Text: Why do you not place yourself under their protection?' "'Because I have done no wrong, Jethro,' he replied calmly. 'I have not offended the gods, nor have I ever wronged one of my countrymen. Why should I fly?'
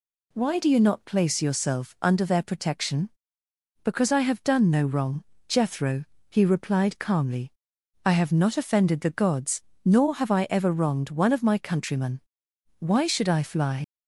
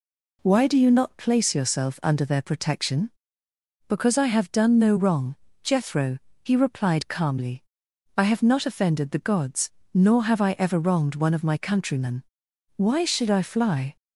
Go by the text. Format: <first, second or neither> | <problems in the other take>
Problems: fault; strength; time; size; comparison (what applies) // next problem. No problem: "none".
second | leaves "fly" unfinished; at 13.8 s; 70 ms